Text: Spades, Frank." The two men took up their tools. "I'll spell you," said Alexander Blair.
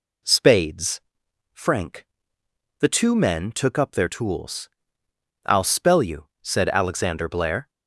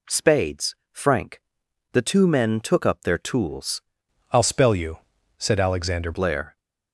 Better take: first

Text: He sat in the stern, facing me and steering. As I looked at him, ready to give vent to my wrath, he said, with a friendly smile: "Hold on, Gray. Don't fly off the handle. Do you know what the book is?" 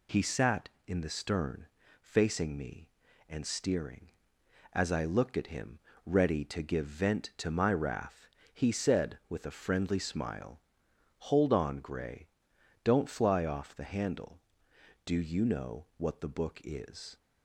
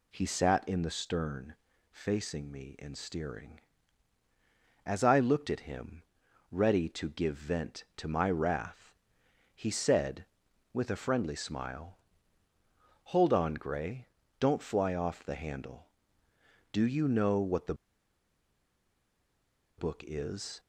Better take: first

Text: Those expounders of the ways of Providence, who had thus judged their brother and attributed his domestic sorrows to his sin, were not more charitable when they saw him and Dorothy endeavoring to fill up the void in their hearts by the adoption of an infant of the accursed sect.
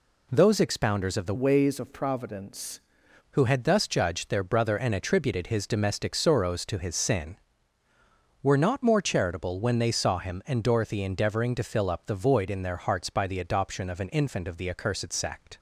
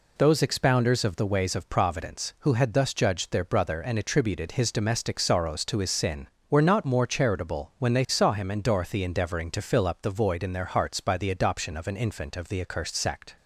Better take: second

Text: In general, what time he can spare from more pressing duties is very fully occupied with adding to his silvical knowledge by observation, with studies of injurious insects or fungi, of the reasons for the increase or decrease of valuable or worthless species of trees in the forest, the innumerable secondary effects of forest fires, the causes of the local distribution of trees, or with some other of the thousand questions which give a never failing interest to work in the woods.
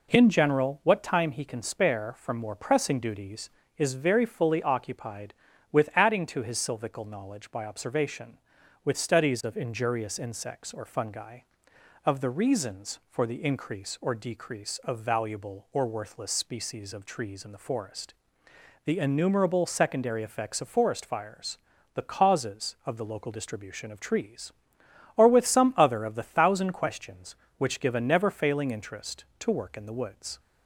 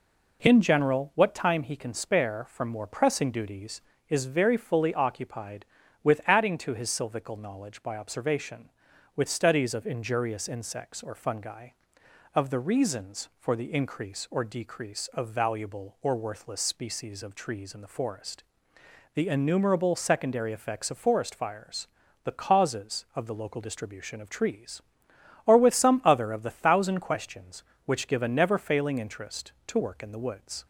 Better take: neither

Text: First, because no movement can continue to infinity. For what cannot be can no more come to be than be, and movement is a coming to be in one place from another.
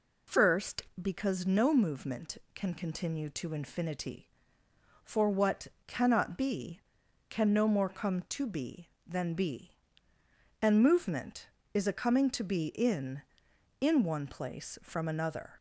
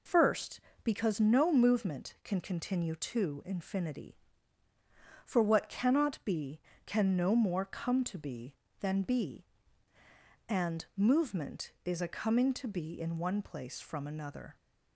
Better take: second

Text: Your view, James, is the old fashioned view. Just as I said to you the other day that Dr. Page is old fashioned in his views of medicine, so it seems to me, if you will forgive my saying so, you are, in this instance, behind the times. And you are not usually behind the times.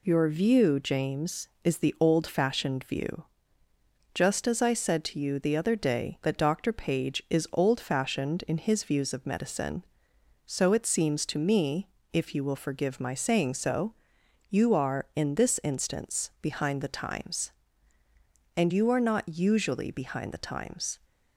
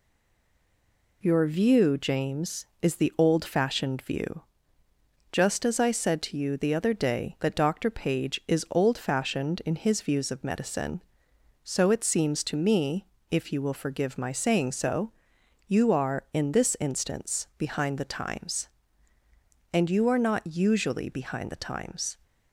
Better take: first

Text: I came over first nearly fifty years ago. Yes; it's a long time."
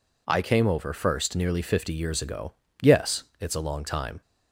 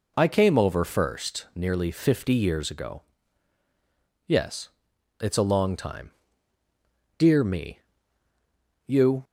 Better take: first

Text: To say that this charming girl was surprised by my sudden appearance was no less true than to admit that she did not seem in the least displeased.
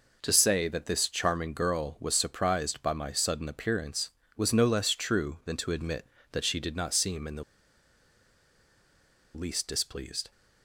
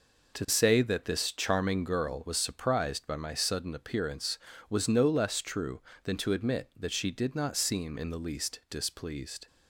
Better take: second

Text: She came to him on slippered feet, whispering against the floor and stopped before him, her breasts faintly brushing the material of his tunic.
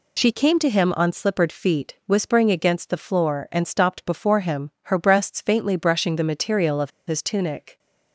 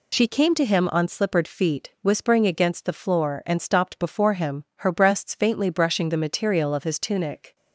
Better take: second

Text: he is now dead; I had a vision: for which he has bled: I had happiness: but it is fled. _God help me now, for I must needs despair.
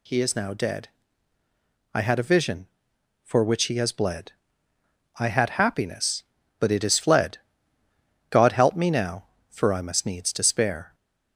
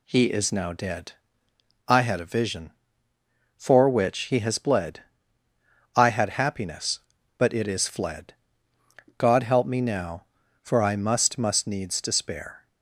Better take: first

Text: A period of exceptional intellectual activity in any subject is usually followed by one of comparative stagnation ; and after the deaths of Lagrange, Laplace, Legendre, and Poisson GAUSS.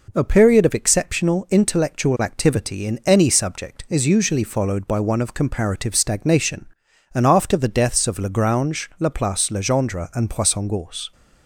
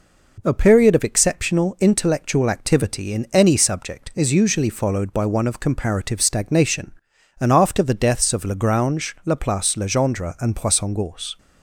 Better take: neither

